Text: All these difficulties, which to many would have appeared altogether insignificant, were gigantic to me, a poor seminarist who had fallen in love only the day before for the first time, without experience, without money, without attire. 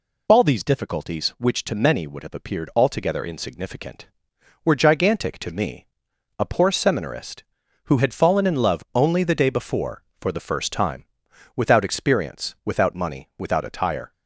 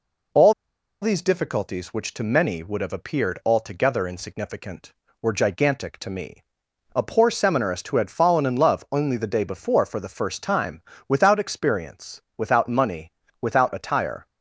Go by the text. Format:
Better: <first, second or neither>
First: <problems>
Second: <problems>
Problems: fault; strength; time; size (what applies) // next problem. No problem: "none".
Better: first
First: none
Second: pauses between "All" and "these"; noticeable; at 0.5 s; 0.48 s long